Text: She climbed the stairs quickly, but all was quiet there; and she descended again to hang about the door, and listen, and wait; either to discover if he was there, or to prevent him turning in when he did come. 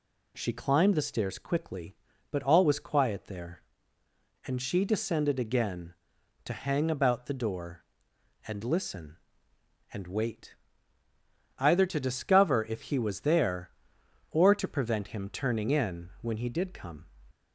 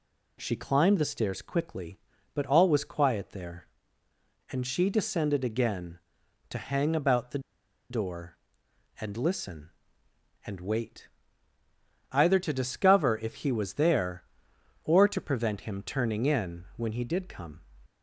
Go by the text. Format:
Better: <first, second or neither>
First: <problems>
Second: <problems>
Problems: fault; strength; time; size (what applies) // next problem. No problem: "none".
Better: first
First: none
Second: pauses between "the" and "door"; noticeable; at 7.3 s; 0.51 s long